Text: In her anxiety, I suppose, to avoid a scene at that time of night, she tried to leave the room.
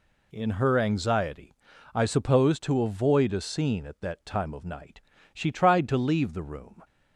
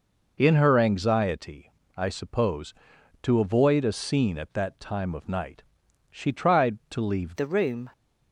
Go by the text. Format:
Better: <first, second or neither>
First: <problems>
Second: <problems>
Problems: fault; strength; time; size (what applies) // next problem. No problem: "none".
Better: first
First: none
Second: changes voice at "the"; from 7.3 s on; 0.6 s long